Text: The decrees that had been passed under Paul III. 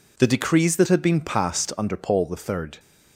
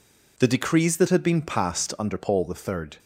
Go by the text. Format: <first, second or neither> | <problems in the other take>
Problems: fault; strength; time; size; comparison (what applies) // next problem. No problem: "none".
neither | none